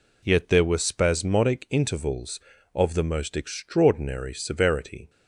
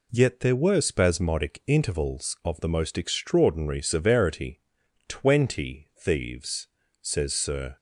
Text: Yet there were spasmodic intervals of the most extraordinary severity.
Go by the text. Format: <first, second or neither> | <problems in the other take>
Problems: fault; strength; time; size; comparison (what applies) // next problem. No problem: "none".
first | goes on to say "Twenty thieves says Sir"; strong; from 5.0 s on; 2.7 s long